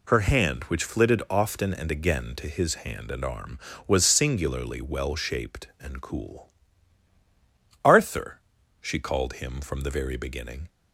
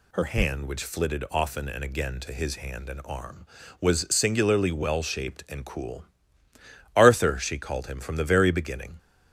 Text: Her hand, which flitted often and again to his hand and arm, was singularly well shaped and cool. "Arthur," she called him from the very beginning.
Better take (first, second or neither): neither